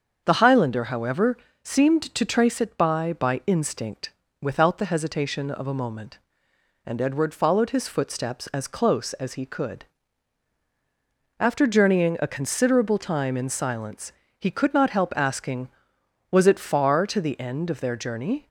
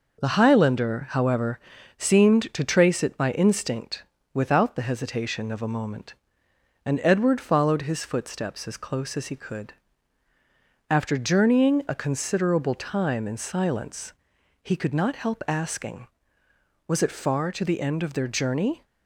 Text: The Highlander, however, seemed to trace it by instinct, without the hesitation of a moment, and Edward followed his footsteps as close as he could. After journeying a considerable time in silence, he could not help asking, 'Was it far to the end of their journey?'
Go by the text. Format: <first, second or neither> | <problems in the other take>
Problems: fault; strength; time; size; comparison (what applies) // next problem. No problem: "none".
second | starts louder than the rest; until 1.2 s; 7 dB // says "by" twice; at 3.1 s